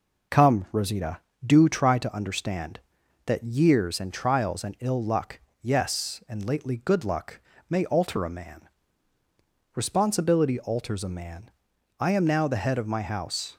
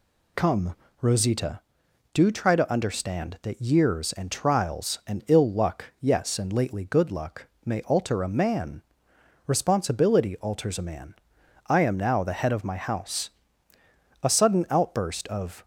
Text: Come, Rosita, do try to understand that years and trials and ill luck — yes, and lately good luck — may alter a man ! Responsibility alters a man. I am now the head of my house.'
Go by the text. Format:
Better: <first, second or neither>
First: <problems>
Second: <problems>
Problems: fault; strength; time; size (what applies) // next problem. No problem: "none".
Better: first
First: none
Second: goes on to say "A sudden outburst of"; from 14.2 s on; 1.4 s long